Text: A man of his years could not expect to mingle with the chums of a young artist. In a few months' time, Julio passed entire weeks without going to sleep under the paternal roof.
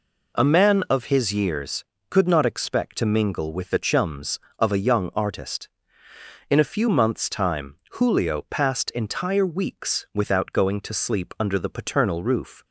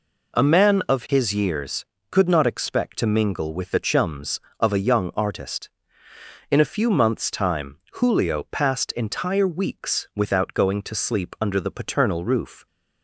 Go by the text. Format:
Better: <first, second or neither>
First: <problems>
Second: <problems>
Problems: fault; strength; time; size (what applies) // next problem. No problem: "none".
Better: neither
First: none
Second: none